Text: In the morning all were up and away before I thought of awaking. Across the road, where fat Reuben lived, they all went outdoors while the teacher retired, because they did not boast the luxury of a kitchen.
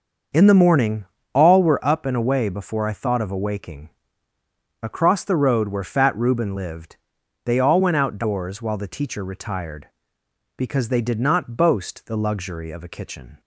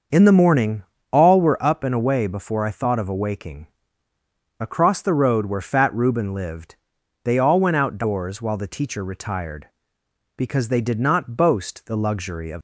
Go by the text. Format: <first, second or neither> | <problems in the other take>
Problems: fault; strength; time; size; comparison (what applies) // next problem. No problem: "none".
first | starts louder than the rest; until 1.4 s; 6.5 dB; also in the first // pauses between "morning" and "all"; slight; at 0.8 s; 0.30 s long; slight in the first // stops before "a kitchen"; at 12.5 s